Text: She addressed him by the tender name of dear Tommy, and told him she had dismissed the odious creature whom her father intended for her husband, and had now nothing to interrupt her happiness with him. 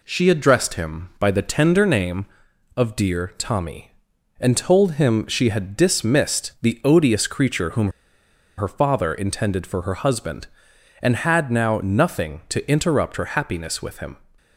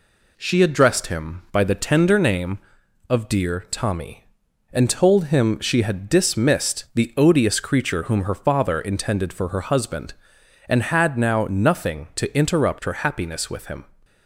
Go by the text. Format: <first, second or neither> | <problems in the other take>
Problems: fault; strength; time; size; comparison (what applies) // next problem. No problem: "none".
second | pauses between "whom" and "her"; noticeable; at 7.9 s; 0.66 s long